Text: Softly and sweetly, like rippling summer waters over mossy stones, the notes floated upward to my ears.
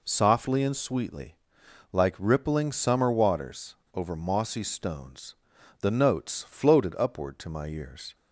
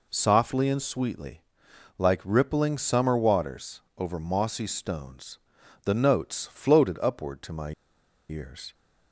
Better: first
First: pauses between "waters" and "over"; slight; at 3.7 s; 0.18 s long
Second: pauses between "waters" and "over"; slight; at 3.8 s; 0.16 s long // pauses between "my" and "ears"; noticeable; at 7.7 s; 0.57 s long

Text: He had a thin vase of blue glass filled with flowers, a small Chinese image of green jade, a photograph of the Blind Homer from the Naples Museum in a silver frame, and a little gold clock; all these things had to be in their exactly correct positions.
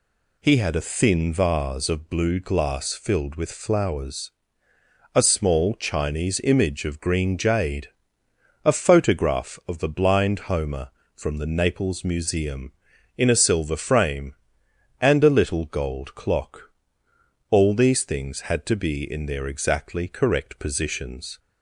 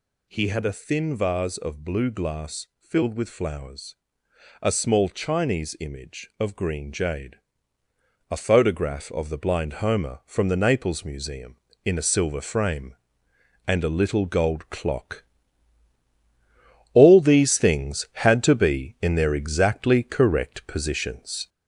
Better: first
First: none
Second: gets louder; slight; throughout; 3 dB

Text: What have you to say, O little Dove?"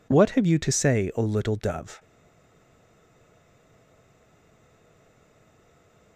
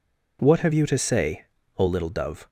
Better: second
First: stays silent after the last word; strong; from 1.9 s on; 4.2 s long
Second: none

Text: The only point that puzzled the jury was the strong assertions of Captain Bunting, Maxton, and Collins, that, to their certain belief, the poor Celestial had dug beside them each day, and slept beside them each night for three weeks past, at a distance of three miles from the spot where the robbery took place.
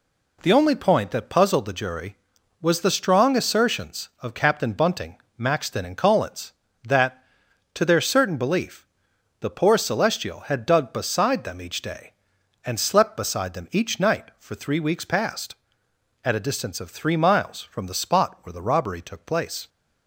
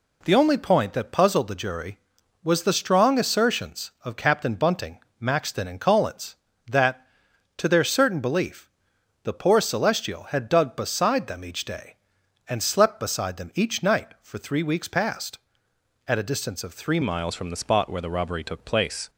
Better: first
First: none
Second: changes voice at "miles"; from 17.0 s on; 2.0 s long

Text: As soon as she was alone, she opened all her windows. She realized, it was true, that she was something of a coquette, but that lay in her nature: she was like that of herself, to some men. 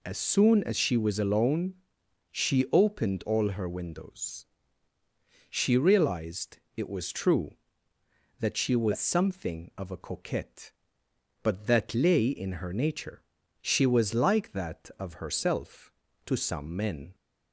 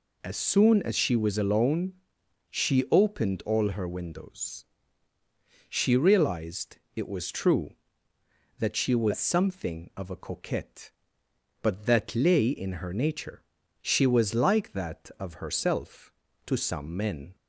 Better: neither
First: none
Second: none

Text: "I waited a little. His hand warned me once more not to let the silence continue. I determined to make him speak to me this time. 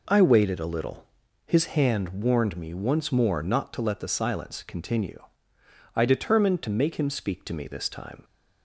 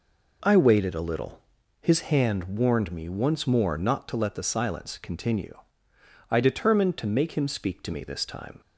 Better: neither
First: none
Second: none

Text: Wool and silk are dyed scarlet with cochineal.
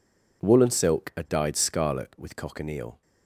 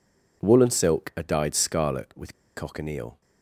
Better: first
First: none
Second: pauses between "with" and "cochineal"; slight; at 2.3 s; 0.22 s long

